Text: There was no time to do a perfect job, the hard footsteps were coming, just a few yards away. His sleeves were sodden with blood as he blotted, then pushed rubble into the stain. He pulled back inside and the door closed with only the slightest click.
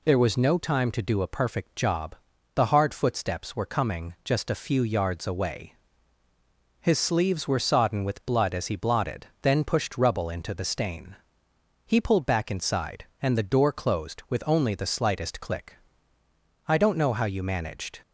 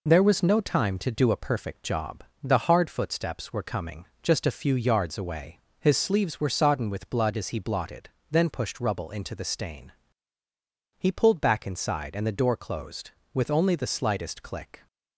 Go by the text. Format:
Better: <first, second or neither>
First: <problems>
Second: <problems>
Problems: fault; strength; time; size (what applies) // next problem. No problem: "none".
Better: second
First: goes on to say "I don't know how you managed"; from 16.6 s on; 1.3 s long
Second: none